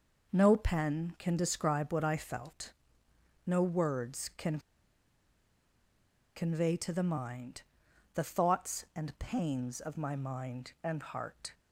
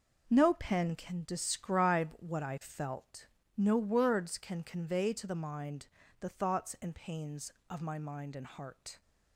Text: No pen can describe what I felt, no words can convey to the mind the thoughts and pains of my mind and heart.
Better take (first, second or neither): second